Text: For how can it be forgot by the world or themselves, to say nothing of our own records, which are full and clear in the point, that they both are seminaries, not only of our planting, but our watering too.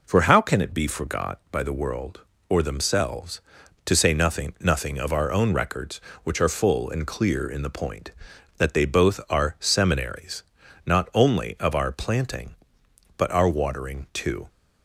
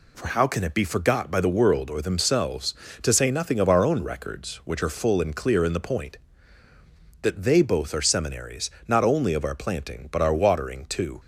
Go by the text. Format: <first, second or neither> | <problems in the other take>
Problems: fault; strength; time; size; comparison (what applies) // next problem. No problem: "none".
second | says "nothing" twice; at 4.5 s